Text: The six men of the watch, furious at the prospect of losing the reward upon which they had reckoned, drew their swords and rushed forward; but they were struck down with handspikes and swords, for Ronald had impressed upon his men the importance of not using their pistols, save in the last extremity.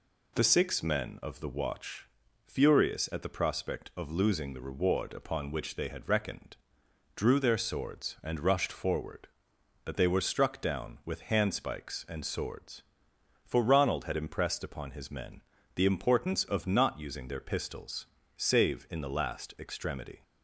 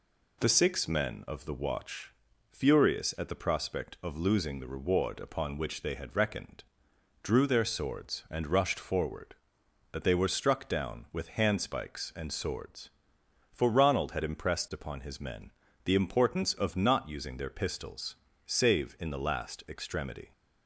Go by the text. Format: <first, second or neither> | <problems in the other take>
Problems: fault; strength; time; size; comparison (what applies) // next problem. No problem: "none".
neither | pauses between "men" and "the"; slight; the same in both